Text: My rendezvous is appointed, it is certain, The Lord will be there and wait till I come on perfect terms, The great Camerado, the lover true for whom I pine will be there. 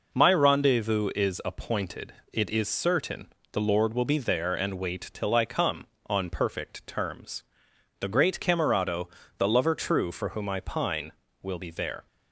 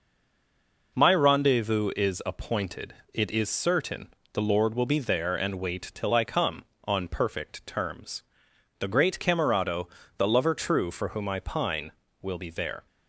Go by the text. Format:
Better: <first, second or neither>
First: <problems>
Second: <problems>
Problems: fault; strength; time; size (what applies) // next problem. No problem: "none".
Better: first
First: none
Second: stays silent before the first word; slight; until 0.9 s; 0.9 s long